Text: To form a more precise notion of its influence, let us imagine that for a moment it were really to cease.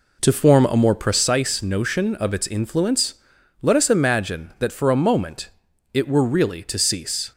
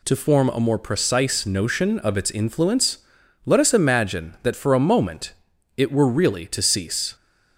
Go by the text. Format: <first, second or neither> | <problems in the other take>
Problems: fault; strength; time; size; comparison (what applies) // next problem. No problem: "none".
second | starts louder than the rest; until 1.3 s; 3.5 dB // pauses between "moment" and "it"; noticeable; at 5.4 s; 0.46 s long; noticeable in the second